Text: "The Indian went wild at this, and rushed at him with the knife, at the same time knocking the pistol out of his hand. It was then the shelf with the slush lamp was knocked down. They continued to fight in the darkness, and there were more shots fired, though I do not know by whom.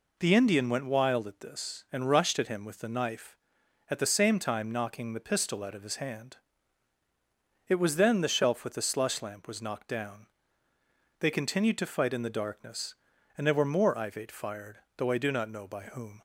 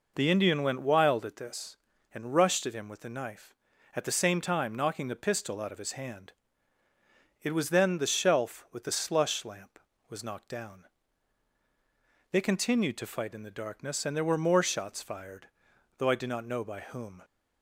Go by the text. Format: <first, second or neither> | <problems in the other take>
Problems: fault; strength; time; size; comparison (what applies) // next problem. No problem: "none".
second | says "ivate" for "shots"; at 13.9 s